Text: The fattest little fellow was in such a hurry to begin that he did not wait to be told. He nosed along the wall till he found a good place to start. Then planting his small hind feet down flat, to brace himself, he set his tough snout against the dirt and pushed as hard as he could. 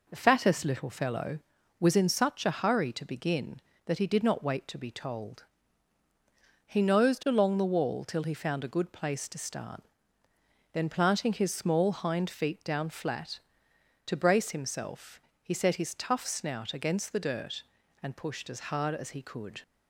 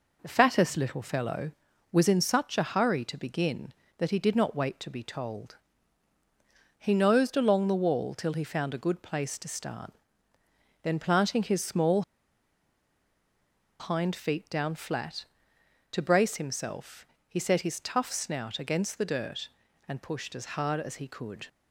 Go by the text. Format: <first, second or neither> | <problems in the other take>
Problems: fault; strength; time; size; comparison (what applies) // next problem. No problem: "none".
first | pauses between "small" and "hind"; strong; at 12.0 s; 1.7 s long